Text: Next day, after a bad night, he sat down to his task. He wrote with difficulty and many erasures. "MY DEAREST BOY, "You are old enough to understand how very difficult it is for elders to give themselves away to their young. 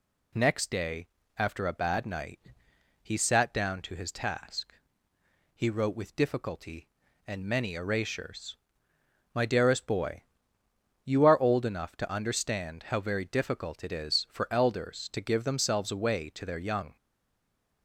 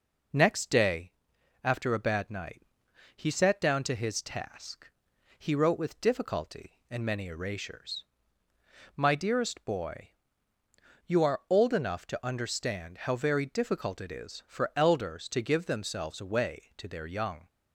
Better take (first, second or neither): second